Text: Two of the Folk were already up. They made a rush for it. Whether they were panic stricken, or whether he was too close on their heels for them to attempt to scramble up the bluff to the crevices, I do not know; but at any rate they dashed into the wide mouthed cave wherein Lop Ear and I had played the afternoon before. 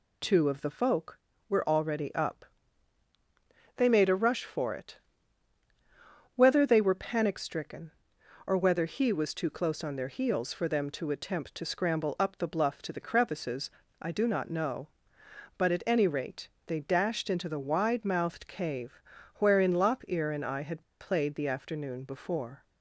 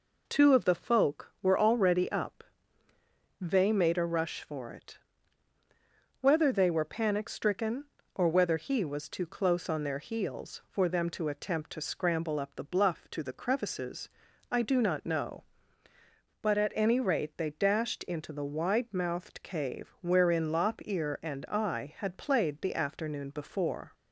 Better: second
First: pauses between "rate" and "they"; slight; at 16.4 s; 0.20 s long // pauses between "cave" and "wherein"; slight; at 19.0 s; 0.36 s long // pauses between "had" and "played"; slight; at 20.8 s; 0.19 s long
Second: none

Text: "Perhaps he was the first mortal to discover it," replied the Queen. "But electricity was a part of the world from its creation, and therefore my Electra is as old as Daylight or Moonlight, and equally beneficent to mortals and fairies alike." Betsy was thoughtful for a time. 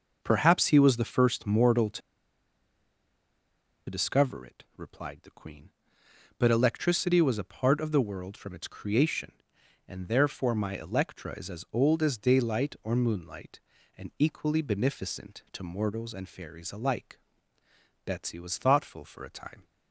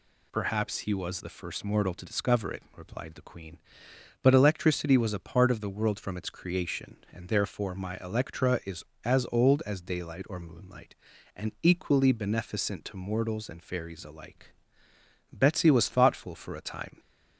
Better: second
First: pauses between "to" and "discover"; strong; at 2.0 s; 1.8 s long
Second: none

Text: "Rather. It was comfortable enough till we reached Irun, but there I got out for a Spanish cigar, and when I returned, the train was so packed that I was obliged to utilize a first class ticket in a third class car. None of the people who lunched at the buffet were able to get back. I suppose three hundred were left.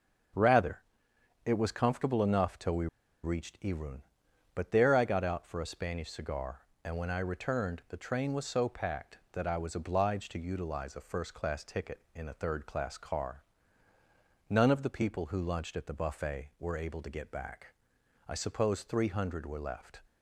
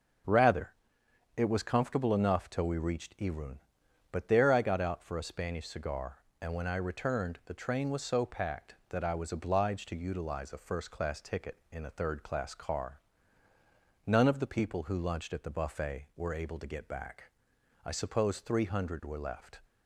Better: second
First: starts louder than the rest; until 1.9 s; 6.5 dB // pauses between "we" and "reached"; at 2.8 s; 0.37 s long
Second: starts louder than the rest; until 1.9 s; 6.5 dB

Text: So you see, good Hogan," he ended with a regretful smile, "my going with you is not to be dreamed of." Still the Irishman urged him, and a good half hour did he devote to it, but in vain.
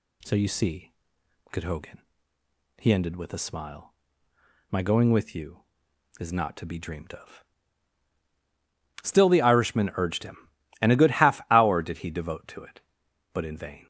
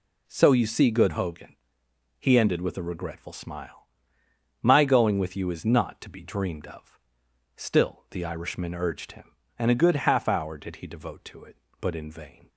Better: second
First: skips "regretful"; at 3.3 s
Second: none

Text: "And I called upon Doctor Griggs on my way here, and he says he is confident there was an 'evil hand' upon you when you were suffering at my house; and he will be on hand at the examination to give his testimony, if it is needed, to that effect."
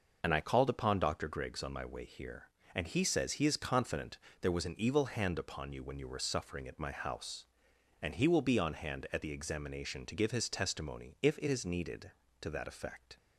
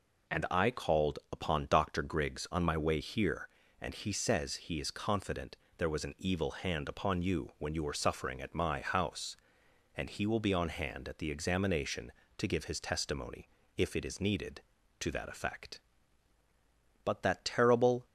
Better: first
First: pauses between "confident" and "there"; slight; at 4.1 s; 0.22 s long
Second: pauses between "confident" and "there"; slight; at 5.5 s; 0.20 s long // goes on to say "But that terrible"; noticeable; from 17.0 s on; 1.0 s long

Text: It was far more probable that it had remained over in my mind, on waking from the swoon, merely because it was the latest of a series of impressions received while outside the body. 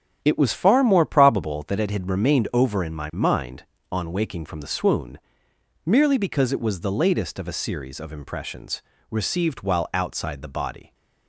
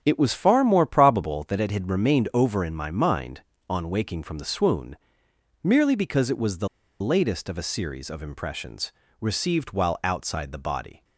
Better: first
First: starts louder than the rest; strong; until 1.2 s; 9 dB // pauses between "impressions" and "received"; slight; at 8.8 s; 0.28 s long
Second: starts louder than the rest; strong; until 1.0 s; 9 dB // pauses between "the" and "latest"; slight; at 6.6 s; 0.34 s long // pauses between "impressions" and "received"; slight; at 8.9 s; 0.28 s long

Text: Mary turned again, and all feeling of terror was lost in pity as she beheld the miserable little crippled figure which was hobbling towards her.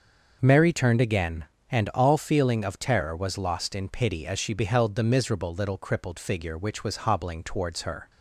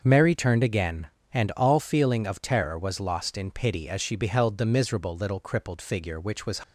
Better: first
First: starts louder than the rest; noticeable; until 1.4 s; 6 dB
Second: starts louder than the rest; until 1.0 s; 6.5 dB // stops before "hobbling towards her"; at 6.6 s

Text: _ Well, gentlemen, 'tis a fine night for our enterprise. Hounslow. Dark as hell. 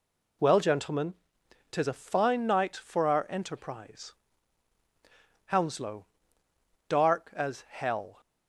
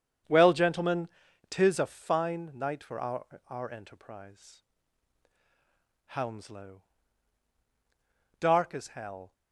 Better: first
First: none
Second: starts louder than the rest; strong; until 1.6 s; 8 dB // says "our" twice; at 3.4 s

